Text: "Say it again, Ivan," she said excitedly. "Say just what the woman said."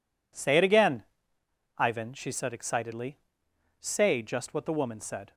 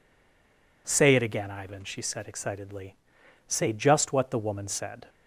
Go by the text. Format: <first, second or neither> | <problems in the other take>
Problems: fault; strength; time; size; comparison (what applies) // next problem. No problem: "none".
first | stays silent before the first word; slight; until 0.8 s; 0.8 s long